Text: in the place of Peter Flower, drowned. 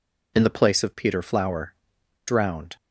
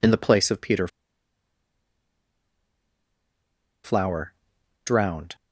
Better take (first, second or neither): first